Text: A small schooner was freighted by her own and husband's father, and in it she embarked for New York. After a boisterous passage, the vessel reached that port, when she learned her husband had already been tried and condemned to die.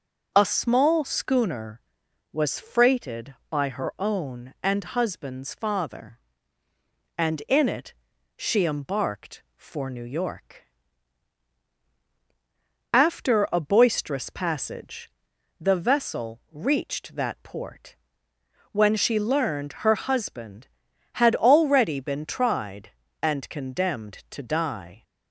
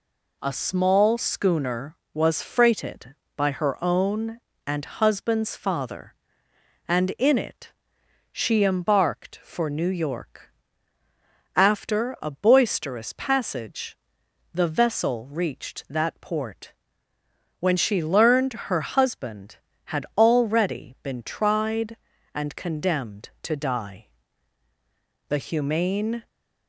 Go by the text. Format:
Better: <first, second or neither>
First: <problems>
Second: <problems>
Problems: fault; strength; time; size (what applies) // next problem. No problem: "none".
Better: first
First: pauses between "it" and "she"; at 7.9 s; 0.42 s long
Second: pauses between "it" and "she"; noticeable; at 7.7 s; 0.58 s long // goes on to say "The humane"; noticeable; from 25.2 s on; 0.98 s long